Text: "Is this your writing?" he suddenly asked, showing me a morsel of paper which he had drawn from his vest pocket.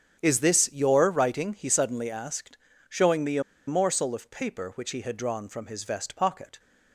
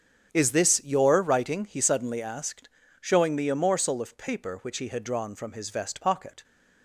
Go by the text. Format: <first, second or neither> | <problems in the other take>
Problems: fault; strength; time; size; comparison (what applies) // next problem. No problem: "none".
second | starts louder than the rest; strong; until 1.2 s; 8.5 dB; strong in the second // pauses between "a" and "morsel"; slight; at 3.4 s; 0.26 s long